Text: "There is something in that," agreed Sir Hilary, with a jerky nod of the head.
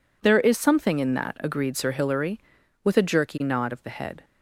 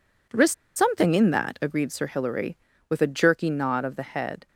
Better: first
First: none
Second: pauses between "is" and "something"; slight; at 0.5 s; 0.24 s long

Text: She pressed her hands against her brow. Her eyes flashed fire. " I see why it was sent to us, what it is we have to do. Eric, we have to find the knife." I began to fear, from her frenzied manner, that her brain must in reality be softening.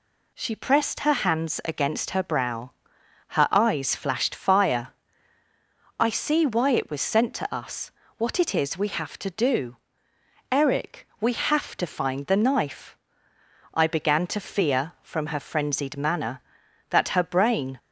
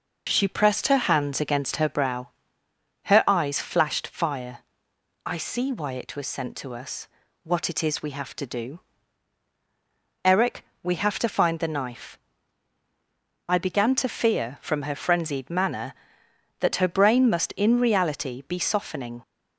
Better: second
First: stops before "must in reality be softening"; at 17.7 s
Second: none

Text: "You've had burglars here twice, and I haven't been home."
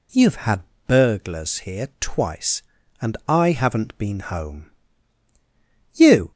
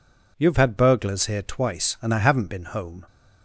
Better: second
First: pauses between "had" and "burglars"; slight; at 0.6 s; 0.24 s long // goes on to say "You"; slight; from 5.9 s on; 0.38 s long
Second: none

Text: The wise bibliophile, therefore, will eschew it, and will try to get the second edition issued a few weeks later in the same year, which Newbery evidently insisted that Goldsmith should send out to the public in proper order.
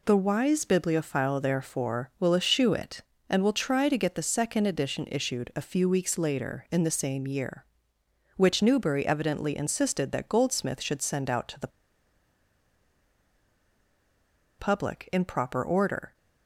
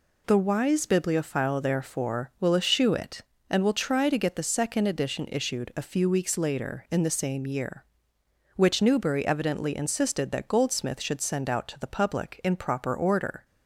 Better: second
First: pauses between "the" and "public"; strong; at 11.7 s; 2.8 s long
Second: none

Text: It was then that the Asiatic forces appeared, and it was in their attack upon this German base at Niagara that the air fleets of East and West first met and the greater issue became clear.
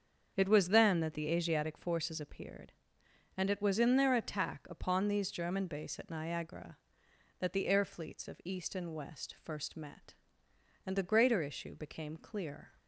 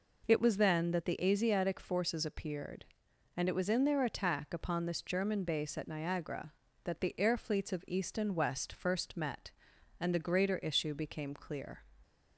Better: second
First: starts louder than the rest; until 1.3 s; 7 dB // says "these" for "this"; at 5.0 s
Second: none

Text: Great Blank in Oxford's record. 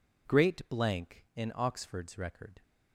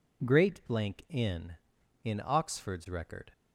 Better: first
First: none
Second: says "in" twice; at 2.0 s

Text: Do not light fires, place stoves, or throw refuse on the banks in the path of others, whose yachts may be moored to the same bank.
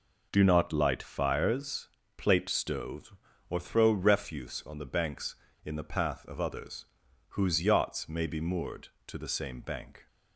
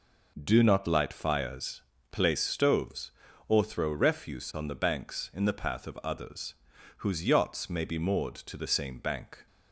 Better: second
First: says "plate" for "place"; at 2.1 s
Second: none

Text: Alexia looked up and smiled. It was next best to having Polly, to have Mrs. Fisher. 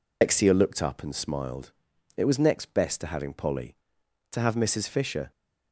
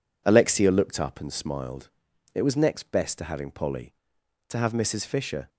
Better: second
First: loses the start of "Alexia"; at 0.2 s; 135 ms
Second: none

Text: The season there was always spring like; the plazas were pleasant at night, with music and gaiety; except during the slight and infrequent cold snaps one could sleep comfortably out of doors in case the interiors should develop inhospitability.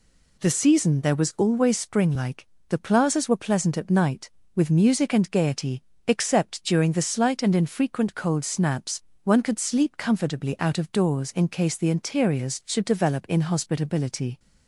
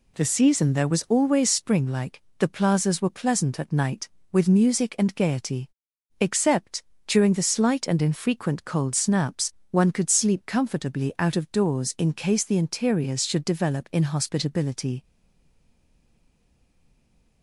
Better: first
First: pauses between "snaps" and "one"; slight; at 9.0 s; 0.22 s long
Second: pauses between "except" and "during"; slight; at 6.8 s; 0.24 s long // pauses between "snaps" and "one"; slight; at 9.5 s; 0.16 s long // stays silent after the last word; from 15.0 s on; 2.4 s long

